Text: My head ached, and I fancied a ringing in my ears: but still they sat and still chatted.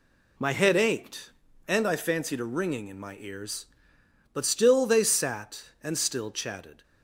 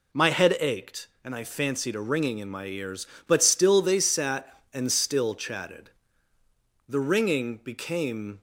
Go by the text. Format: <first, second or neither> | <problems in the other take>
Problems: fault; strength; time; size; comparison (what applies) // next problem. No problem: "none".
first | goes on to say "The ringing became"; from 6.8 s on; 1.5 s long